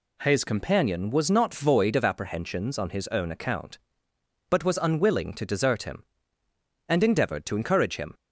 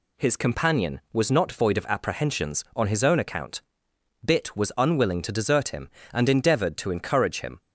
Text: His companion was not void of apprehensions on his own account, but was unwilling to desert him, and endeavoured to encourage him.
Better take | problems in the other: first | says "bit" for "but"; at 4.2 s

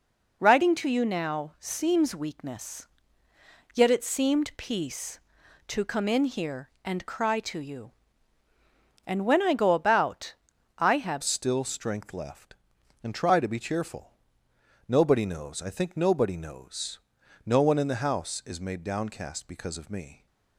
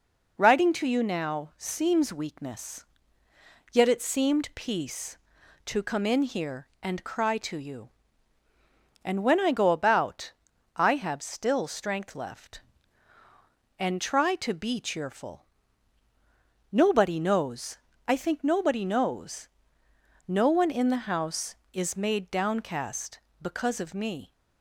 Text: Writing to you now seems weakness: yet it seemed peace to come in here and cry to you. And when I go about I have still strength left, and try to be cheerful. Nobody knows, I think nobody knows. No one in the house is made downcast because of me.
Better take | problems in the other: second | pauses between "about" and "I"; at 10.3 s; 0.44 s long; also in the second // changes voice at "still"; from 11.2 s on; 9.0 s long

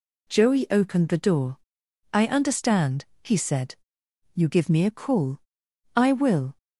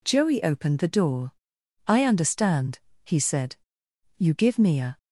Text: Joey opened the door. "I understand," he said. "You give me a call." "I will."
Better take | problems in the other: first | stops before "call I will"; at 4.9 s

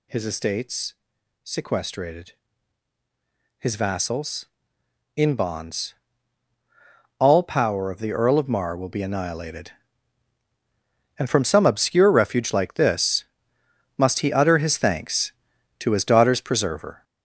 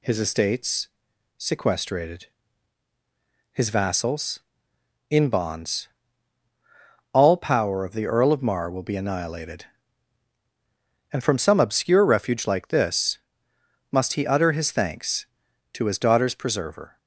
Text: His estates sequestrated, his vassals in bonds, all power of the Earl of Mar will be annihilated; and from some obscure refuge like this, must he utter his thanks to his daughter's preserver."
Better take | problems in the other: second | gets louder; throughout; 6.5 dB // pauses between "estates" and "sequestrated"; noticeable; at 0.9 s; 0.48 s long; noticeable in the second

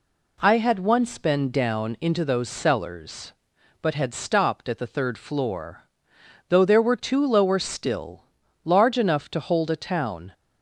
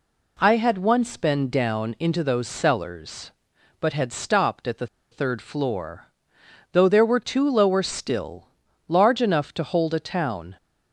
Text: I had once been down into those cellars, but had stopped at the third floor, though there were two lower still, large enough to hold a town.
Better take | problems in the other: first | pauses between "the" and "third"; slight; at 4.8 s; 0.25 s long

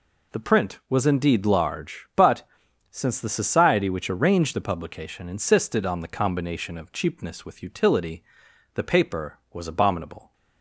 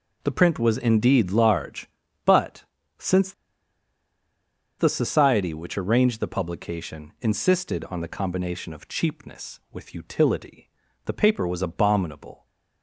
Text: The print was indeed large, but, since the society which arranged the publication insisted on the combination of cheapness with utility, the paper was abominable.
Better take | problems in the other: first | pauses between "since" and "the"; strong; at 3.3 s; 1.4 s long

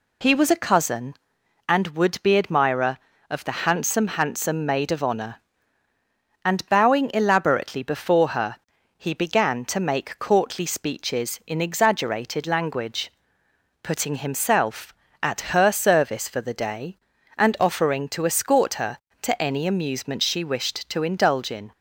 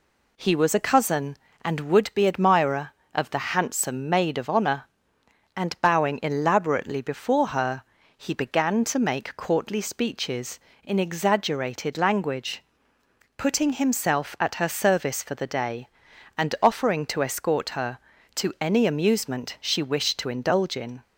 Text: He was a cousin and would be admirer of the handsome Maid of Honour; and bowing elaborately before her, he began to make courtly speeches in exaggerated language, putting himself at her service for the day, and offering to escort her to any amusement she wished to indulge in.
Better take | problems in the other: second | says "handsome" twice; at 4.0 s

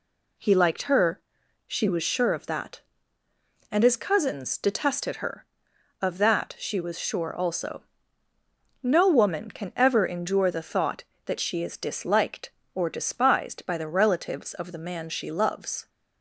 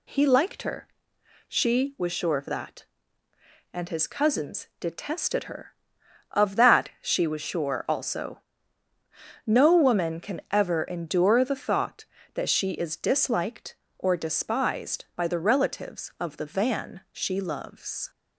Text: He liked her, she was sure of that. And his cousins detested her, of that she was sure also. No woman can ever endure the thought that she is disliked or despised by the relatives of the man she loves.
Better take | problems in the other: first | says "van" for "man"; at 16.4 s

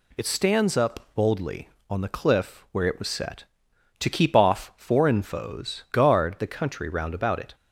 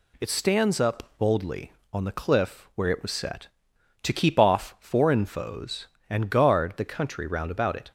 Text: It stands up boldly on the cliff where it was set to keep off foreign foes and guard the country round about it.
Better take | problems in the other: second | skips "and"; at 5.8 s

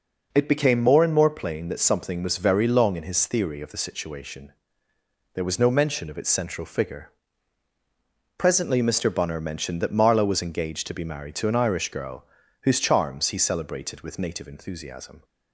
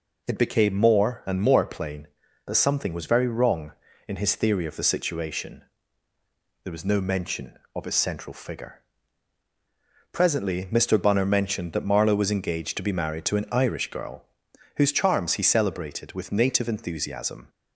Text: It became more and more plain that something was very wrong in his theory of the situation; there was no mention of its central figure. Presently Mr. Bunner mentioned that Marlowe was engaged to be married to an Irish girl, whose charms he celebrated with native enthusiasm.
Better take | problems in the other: second | says "long" for "wrong"; at 2.6 s

